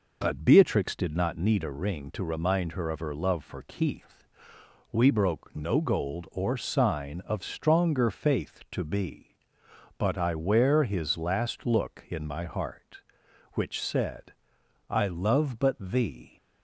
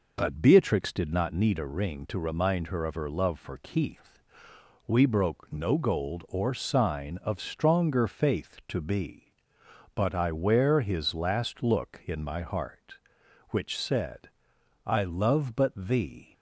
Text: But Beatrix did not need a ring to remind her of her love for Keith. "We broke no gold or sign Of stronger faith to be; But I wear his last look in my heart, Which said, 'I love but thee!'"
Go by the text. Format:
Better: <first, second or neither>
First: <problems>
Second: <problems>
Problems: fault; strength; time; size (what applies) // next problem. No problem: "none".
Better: neither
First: none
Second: none